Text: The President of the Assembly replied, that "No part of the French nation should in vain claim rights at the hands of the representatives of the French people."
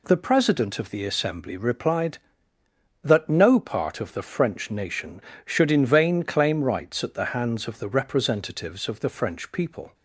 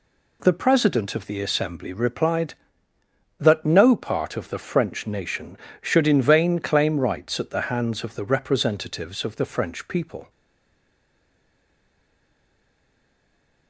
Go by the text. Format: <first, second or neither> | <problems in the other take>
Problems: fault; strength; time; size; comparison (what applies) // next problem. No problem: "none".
first | stays silent after the last word; strong; from 10.2 s on; 3.4 s long